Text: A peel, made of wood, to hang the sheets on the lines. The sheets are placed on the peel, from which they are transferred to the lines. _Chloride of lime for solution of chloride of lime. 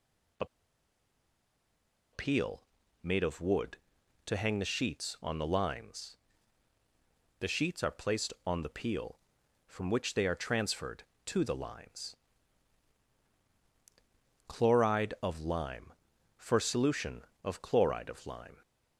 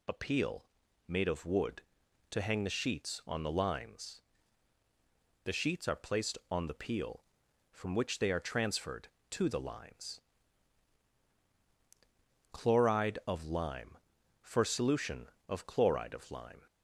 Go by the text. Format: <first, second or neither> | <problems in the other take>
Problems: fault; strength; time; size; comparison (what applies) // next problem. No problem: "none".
second | pauses between "A" and "peel"; strong; at 0.4 s; 1.6 s long